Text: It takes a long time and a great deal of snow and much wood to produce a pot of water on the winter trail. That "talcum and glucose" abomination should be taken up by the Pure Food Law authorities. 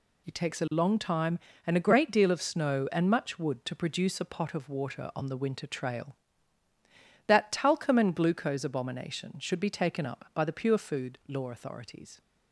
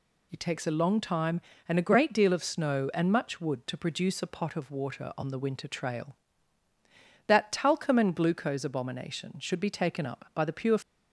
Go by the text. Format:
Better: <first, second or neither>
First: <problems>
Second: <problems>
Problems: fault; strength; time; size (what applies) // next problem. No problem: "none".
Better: first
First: none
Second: stops before "Food Law authorities"; at 10.8 s